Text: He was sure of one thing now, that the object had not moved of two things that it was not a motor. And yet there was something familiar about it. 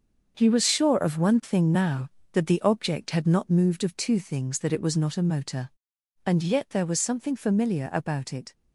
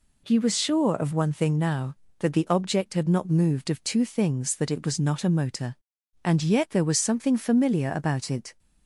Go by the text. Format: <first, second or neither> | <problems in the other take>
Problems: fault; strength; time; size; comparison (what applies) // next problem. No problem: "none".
second | gets quieter; strong; throughout; 9 dB